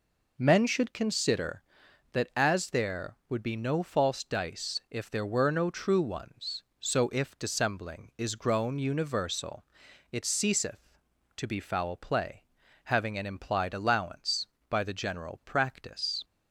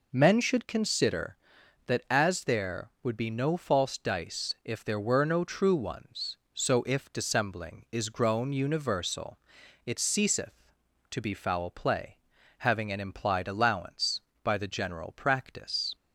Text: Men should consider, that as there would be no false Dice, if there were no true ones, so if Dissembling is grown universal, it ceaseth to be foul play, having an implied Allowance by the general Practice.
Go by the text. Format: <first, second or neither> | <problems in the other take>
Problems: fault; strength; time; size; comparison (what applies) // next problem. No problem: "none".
neither | none